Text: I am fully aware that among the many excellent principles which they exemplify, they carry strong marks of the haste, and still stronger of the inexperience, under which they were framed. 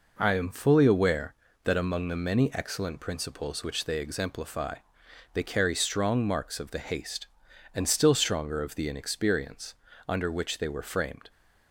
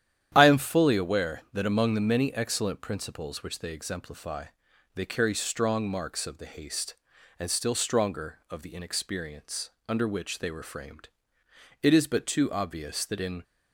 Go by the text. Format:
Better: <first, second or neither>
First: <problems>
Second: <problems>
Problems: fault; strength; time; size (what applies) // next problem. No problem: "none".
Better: first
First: none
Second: starts louder than the rest; strong; until 1.3 s; 10.5 dB // goes on to say "It is but too obvious that in"; from 11.8 s on; 1.6 s long